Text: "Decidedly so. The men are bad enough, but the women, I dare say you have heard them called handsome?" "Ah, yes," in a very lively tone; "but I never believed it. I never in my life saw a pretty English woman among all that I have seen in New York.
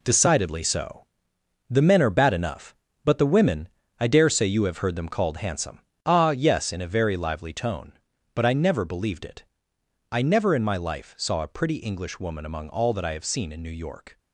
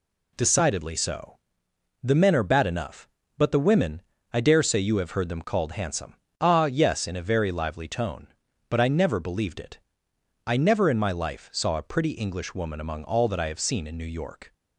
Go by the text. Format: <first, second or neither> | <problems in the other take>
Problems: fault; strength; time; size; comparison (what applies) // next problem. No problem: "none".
second | gets quieter; strong; throughout; 9 dB